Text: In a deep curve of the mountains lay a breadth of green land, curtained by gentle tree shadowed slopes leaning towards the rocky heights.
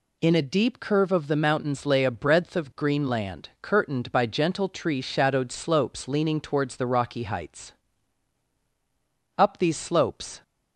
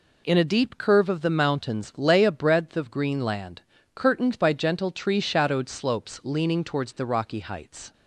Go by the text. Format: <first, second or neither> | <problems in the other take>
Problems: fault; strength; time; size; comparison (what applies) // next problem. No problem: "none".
second | goes on to say "Up these slopes"; noticeable; from 9.3 s on; 1.0 s long